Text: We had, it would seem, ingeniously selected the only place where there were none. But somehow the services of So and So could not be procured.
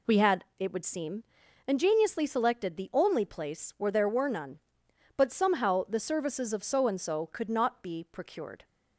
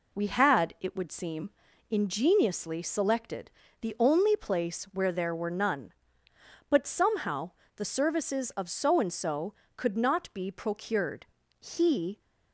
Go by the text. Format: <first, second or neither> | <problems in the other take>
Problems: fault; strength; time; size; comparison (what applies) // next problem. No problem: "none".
first | pauses between "selected" and "the"; slight; at 3.4 s; 0.30 s long // pauses between "somehow" and "the"; slight; at 7.5 s; 0.24 s long // goes on to say "He"; from 11.6 s on; 0.58 s long